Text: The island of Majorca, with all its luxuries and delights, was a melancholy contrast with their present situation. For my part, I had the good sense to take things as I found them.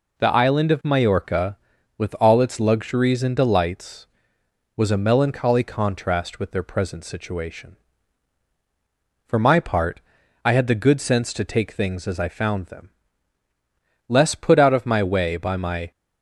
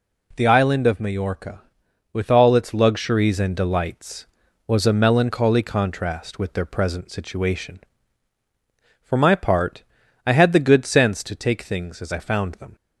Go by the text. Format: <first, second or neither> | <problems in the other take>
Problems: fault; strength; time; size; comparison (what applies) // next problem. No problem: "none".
second | goes on to say "Less put out of my way by my"; strong; from 14.0 s on; 1.8 s long